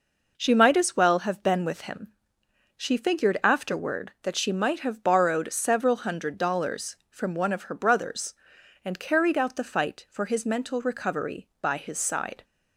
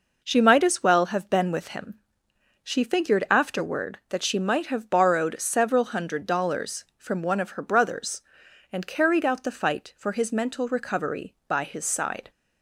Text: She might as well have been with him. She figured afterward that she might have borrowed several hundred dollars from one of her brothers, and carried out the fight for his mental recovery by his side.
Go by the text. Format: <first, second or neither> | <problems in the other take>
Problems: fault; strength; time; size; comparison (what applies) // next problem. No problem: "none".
neither | none